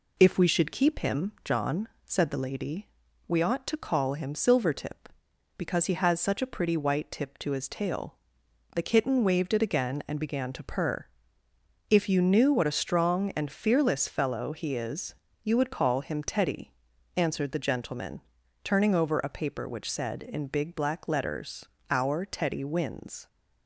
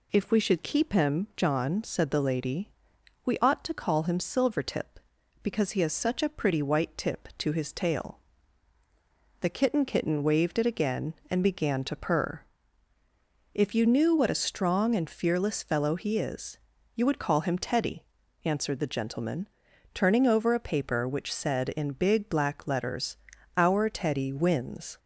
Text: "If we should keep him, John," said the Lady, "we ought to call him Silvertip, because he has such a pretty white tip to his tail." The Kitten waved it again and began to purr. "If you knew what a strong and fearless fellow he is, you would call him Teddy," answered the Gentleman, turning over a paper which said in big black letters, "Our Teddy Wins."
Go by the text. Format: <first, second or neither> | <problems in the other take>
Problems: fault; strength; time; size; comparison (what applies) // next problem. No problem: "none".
first | says "Kitten" twice; at 9.8 s